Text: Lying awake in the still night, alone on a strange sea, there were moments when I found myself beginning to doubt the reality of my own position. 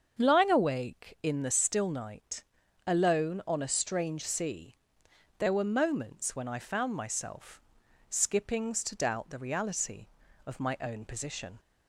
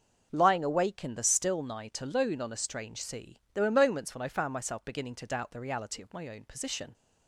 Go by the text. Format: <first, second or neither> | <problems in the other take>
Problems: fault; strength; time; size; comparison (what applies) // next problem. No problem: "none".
second | starts louder than the rest; until 1.2 s; 7 dB; also in the second // says "skippings" for "beginning"; at 8.0 s